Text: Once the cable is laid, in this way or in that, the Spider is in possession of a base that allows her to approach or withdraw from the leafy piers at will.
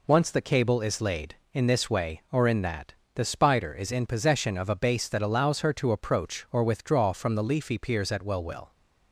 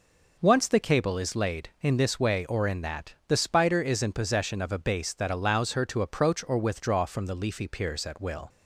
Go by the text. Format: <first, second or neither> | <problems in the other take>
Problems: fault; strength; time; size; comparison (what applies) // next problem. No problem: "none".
second | says "will" twice; at 8.4 s